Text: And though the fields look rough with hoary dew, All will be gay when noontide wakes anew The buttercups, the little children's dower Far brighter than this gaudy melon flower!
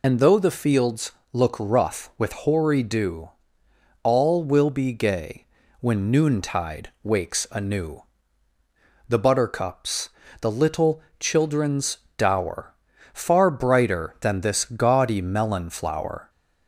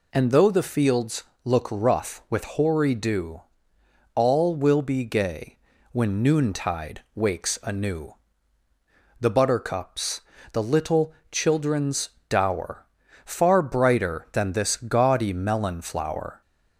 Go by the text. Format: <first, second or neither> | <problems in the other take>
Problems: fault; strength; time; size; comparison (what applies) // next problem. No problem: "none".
second | loses the start of "And"; at 0.0 s; 30 ms // pauses between "fields" and "look"; slight; at 1.1 s; 0.22 s long; slight in the second // pauses between "gay" and "when"; slight; at 5.4 s; 0.36 s long; slight in the second // pauses between "anew" and "The"; at 8.0 s; 1.0 s long; also in the second // pauses between "little" and "children's"; slight; at 11.0 s; 0.18 s long; slight in the second // pauses between "children's" and "dower"; slight; at 11.9 s; 0.20 s long; slight in the second // pauses between "dower" and "Far"; at 12.7 s; 0.40 s long; also in the second